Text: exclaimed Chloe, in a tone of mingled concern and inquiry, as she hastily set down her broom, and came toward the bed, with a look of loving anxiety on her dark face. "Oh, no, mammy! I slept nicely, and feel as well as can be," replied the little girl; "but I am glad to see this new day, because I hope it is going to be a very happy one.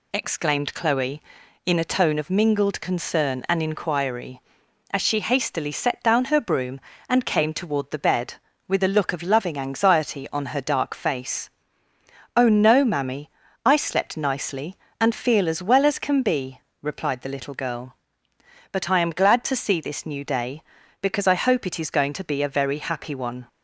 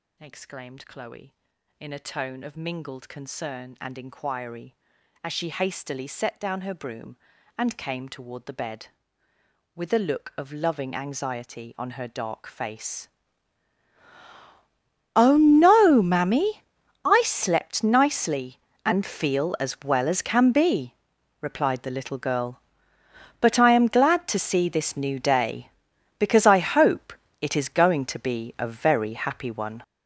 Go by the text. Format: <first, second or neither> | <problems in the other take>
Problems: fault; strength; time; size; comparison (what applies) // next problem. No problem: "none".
first | gets louder; strong; throughout; 11.5 dB // pauses between "hope" and "it"; slight; at 27.1 s; 0.28 s long